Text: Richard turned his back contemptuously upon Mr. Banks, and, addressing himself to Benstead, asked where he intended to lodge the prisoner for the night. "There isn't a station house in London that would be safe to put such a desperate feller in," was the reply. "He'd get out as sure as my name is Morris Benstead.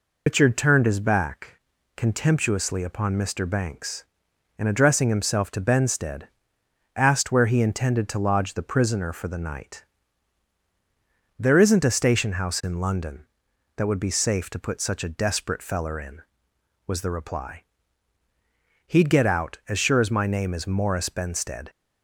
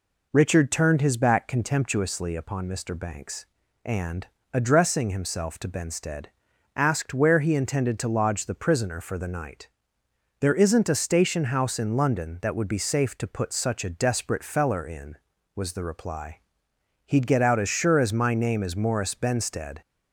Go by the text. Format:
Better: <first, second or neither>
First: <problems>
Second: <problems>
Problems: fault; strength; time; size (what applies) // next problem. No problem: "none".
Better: second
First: loses the start of "Richard"; at 0.2 s; 110 ms // pauses between "back" and "contemptuously"; at 1.5 s; 0.38 s long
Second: none